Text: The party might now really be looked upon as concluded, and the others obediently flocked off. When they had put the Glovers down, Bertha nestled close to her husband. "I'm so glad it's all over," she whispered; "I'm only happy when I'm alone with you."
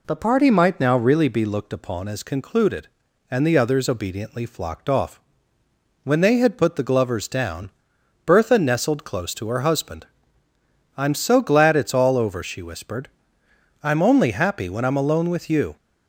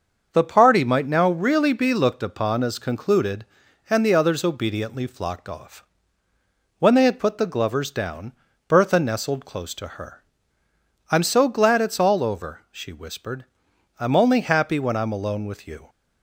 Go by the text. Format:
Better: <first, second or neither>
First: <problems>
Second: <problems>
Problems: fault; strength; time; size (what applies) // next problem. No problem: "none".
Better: first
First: none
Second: starts louder than the rest; until 1.3 s; 6.5 dB // skips "husband"; at 10.6 s